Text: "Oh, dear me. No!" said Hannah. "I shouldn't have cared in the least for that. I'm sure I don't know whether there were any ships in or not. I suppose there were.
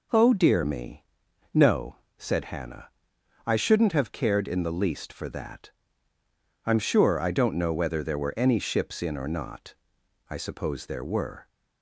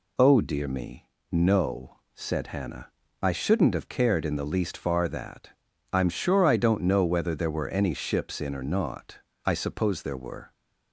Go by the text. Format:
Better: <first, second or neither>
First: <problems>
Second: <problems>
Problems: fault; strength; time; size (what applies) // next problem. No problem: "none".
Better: first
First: none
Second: says "far" for "for"; at 4.7 s